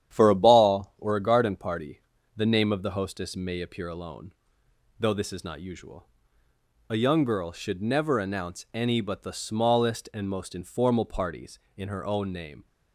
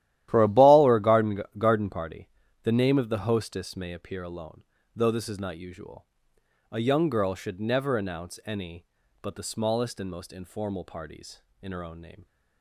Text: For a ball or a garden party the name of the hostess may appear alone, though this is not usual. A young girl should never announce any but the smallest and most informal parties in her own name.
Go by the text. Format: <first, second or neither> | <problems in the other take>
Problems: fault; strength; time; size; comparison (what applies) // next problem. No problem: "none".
first | starts louder than the rest; strong; until 1.3 s; 13 dB; strong in the first // says "garden" twice; at 1.5 s // pauses between "party" and "the"; slight; at 2.2 s; 0.34 s long; slight in the first